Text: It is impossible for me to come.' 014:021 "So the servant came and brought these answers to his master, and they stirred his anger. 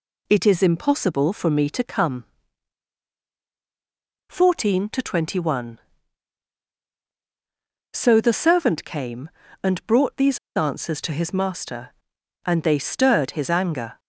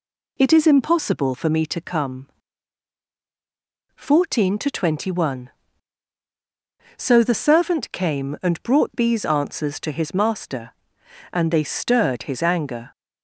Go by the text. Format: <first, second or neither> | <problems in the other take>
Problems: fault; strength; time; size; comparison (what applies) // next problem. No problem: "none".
second | pauses between "these" and "answers"; slight; at 10.3 s; 0.18 s long